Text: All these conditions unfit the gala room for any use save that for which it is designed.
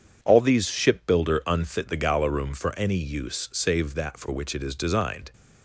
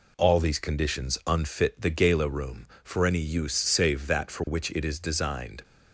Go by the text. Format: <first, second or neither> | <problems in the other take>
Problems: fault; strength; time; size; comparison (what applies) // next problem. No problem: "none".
second | says "shipbuilder" for "conditions"; at 0.6 s